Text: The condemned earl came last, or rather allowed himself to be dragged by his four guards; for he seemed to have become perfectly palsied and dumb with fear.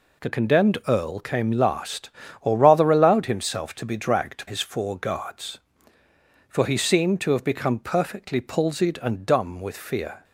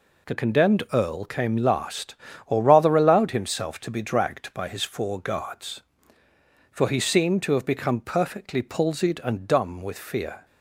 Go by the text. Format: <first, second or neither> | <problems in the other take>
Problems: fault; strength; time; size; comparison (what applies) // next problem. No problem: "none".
second | skips "by"; at 4.4 s